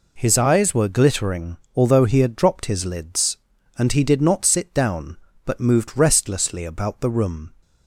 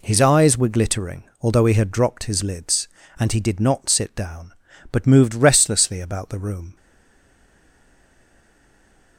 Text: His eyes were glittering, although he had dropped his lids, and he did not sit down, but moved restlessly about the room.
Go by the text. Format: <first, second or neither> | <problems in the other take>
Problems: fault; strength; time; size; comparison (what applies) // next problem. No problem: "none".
first | stays silent after the last word; from 6.7 s on; 2.4 s long